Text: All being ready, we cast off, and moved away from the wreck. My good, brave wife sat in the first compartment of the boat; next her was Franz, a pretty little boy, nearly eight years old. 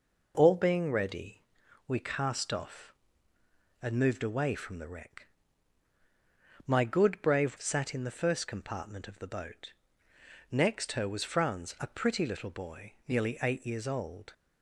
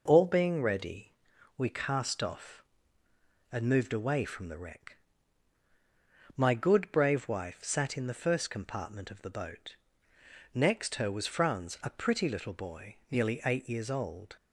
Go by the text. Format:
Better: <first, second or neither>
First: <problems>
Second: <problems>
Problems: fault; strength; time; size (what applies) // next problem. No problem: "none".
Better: second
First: skips "wife"; at 7.5 s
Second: none